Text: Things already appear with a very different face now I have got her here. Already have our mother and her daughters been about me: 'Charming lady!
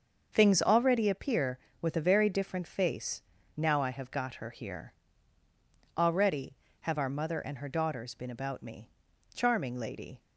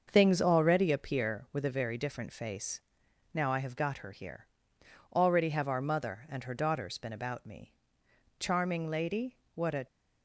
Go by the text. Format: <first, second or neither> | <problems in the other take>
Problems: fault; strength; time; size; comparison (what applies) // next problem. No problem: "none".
first | starts louder than the rest; until 1.1 s; 6.5 dB; also in the first // pauses between "face" and "now"; noticeable; at 2.8 s; 0.54 s long; slight in the first // goes on to say "What a"; slight; from 9.5 s on; 0.30 s long